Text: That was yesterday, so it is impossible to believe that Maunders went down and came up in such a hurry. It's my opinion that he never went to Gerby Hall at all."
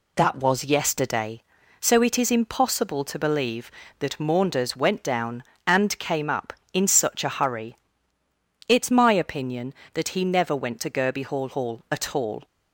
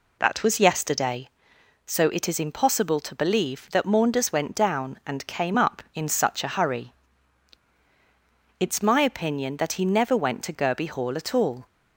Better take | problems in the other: second | says "Hall" twice; at 11.4 s

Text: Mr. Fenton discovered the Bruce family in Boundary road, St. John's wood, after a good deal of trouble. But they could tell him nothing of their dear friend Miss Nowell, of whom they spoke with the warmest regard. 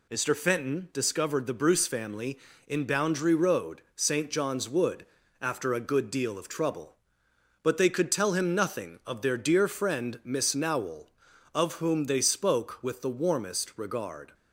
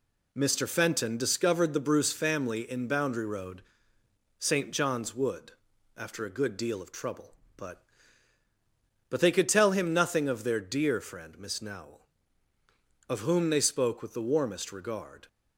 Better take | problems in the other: first | says "But" twice; at 9.0 s

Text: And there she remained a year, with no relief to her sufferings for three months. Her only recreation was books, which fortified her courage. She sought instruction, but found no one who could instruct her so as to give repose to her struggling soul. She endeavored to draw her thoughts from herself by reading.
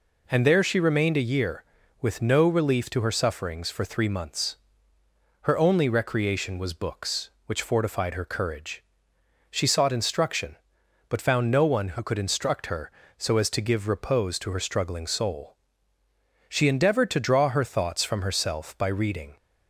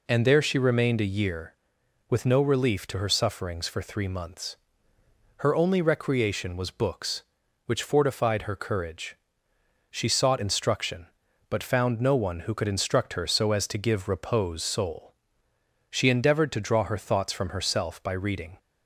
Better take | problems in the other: first | skips "to her struggling"; at 14.6 s

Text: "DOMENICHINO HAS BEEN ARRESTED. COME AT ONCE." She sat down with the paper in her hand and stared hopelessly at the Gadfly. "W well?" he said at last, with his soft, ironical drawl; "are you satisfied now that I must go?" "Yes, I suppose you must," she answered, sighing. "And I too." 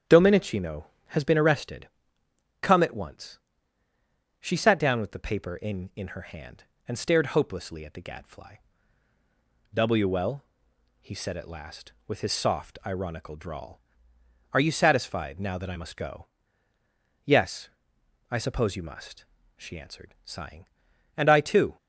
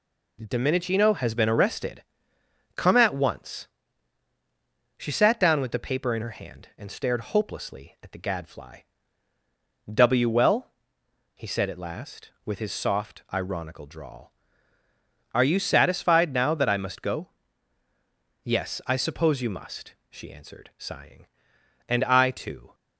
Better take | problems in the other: second | starts louder than the rest; strong; until 1.3 s; 9 dB // says "in" twice; at 5.9 s

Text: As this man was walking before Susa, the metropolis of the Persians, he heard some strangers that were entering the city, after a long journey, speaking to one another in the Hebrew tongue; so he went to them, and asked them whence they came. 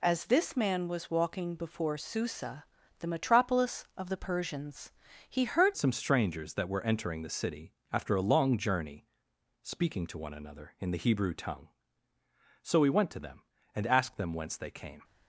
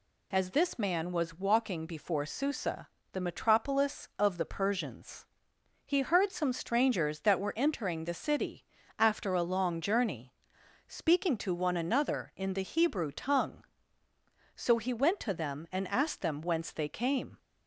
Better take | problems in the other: second | changes voice at "some"; from 5.7 s on; 9.3 s long

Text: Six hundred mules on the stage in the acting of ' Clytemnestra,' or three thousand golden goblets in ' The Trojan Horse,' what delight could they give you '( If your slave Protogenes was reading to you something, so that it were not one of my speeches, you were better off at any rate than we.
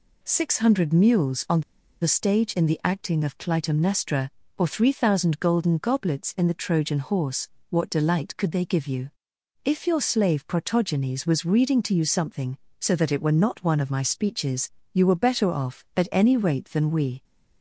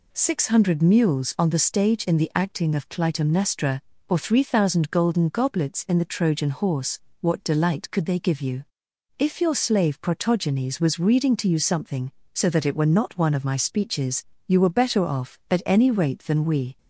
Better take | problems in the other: second | pauses between "on" and "the"; at 1.6 s; 0.40 s long

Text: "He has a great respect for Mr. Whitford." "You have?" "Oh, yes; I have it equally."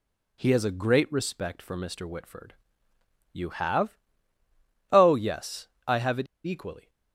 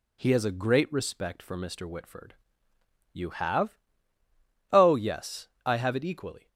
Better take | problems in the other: second | pauses between "it" and "equally"; slight; at 6.2 s; 0.20 s long

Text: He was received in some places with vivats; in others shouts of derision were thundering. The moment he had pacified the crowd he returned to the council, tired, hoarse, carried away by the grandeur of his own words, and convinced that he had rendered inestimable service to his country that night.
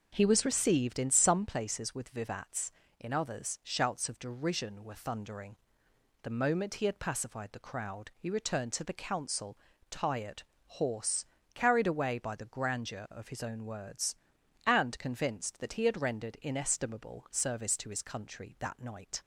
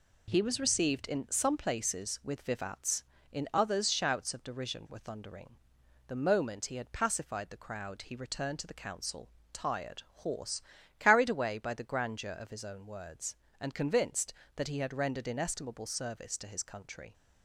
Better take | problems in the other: first | stops before "that night"; at 17.1 s

